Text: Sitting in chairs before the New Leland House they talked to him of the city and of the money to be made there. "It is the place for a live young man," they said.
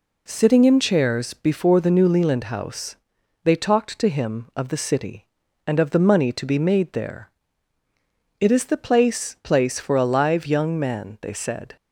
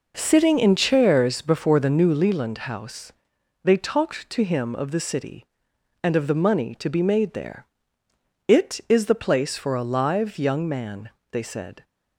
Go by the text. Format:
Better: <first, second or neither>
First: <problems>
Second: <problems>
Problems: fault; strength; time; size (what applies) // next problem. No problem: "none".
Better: second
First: pauses between "House" and "they"; noticeable; at 2.9 s; 0.48 s long // says "place" twice; at 9.4 s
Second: pauses between "House" and "they"; noticeable; at 3.1 s; 0.54 s long